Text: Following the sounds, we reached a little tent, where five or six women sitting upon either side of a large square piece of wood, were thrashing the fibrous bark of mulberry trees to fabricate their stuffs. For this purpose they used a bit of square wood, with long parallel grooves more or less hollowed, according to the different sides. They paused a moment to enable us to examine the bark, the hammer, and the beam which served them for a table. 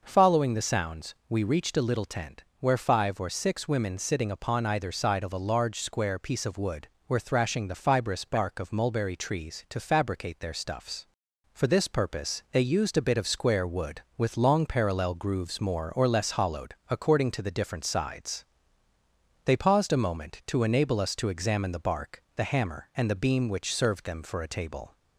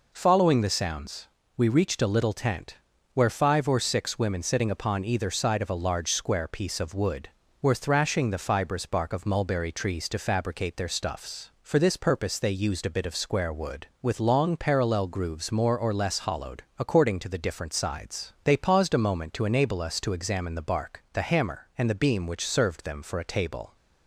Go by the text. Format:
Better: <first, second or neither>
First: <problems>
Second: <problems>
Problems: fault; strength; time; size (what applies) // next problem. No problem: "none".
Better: neither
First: none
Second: none